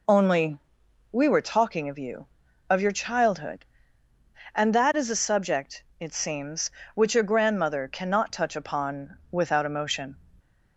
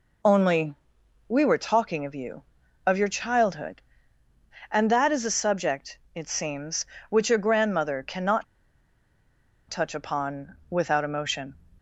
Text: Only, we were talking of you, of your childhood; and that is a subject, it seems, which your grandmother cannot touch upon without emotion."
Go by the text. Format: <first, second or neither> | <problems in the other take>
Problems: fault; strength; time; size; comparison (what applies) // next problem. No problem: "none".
first | pauses between "cannot" and "touch"; strong; at 8.4 s; 1.2 s long // pauses between "upon" and "without"; slight; at 10.5 s; 0.16 s long; slight in the first